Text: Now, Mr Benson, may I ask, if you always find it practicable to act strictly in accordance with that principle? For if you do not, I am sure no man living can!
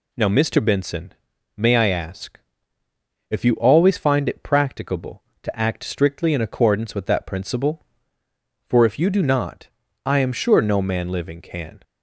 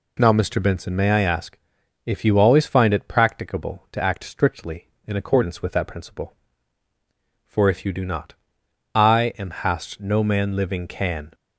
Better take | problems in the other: first | says "hast" for "sure"; at 9.5 s

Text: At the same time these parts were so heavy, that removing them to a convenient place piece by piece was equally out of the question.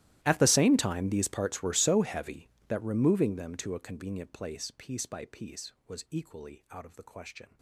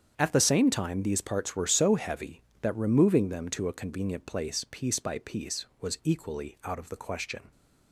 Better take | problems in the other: second | gets quieter; strong; throughout; 24.5 dB // starts louder than the rest; strong; until 1.2 s; 15 dB; strong in the second

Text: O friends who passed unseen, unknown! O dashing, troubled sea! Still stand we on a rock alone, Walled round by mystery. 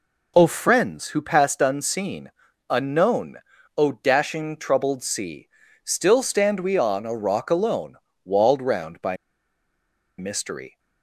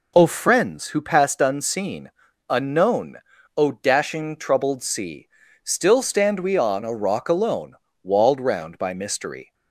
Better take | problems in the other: second | pauses between "by" and "mystery"; at 9.1 s; 1.0 s long

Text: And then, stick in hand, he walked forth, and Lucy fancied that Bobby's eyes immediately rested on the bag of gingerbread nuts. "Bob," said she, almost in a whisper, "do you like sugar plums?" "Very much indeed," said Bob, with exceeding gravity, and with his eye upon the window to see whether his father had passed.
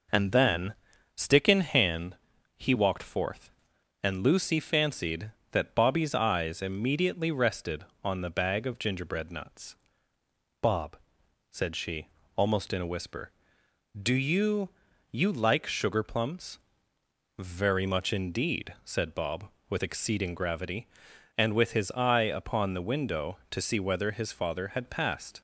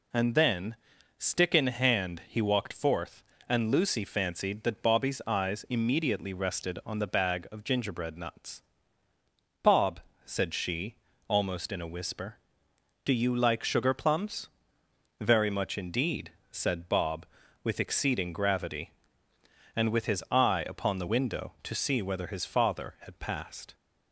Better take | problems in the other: second | says "you" twice; at 15.1 s

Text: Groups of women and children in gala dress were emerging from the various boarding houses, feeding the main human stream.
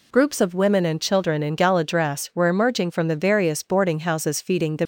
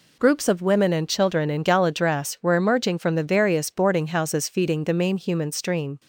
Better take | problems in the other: second | stops before "main human stream"; at 4.8 s

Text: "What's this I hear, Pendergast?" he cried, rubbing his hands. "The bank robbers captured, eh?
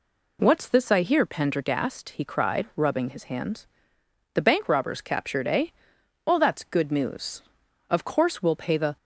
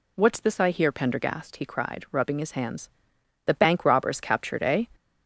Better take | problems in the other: second | goes on to say "Well that's good news Of course we'll pay the"; strong; from 6.2 s on; 2.7 s long

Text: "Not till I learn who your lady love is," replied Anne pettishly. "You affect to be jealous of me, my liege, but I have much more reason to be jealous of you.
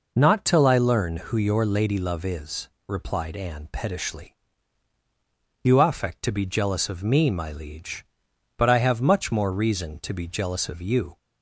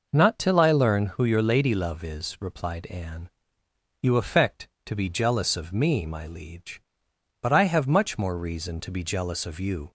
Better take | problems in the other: first | skips "pettishly"; at 3.6 s

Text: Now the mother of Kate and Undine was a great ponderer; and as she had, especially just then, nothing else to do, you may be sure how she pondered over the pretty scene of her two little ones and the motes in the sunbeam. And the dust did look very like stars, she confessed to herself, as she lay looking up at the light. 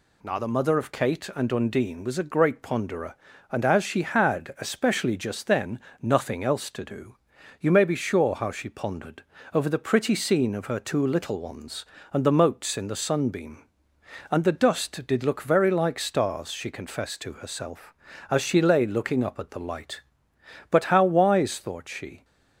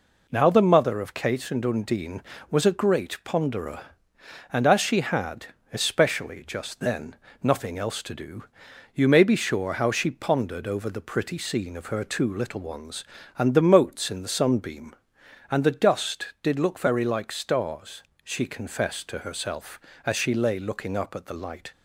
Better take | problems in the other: second | pauses between "pondered" and "over"; slight; at 9.2 s; 0.30 s long // goes on to say "But how wise thought she"; from 20.7 s on; 1.5 s long

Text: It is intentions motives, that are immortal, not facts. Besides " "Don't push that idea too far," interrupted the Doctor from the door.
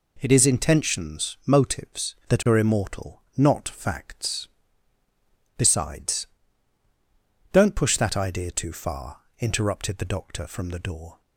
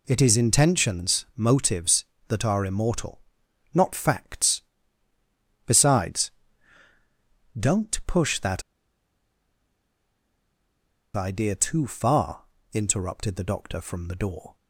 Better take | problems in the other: first | pauses between "that" and "idea"; strong; at 8.6 s; 2.5 s long

